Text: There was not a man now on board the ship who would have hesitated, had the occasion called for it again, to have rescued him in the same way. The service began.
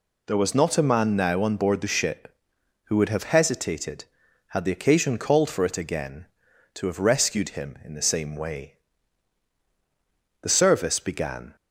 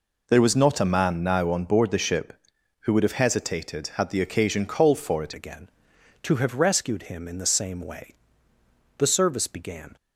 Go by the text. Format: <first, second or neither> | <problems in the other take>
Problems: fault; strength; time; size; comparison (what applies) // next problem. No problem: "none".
first | changes voice at "again"; from 5.3 s on; 4.6 s long